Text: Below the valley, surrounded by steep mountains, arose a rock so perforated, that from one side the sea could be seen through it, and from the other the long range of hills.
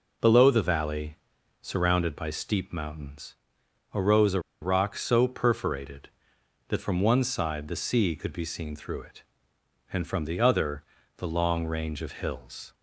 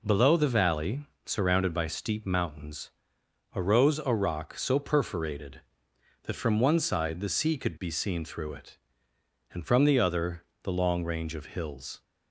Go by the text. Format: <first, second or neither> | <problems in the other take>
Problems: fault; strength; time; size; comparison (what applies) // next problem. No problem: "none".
second | pauses between "a" and "rock"; slight; at 4.3 s; 0.21 s long // pauses between "other" and "the"; slight; at 10.8 s; 0.34 s long; slight in the second